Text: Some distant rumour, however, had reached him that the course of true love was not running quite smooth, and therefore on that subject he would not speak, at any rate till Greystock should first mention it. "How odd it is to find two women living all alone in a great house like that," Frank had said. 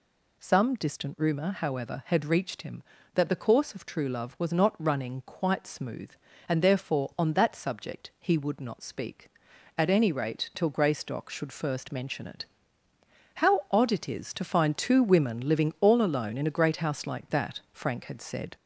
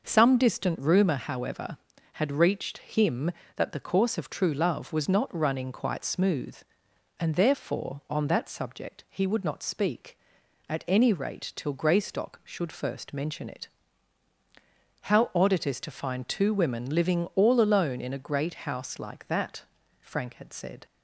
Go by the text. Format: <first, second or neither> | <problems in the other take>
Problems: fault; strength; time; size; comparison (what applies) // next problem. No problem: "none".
second | gets louder; slight; throughout; 3 dB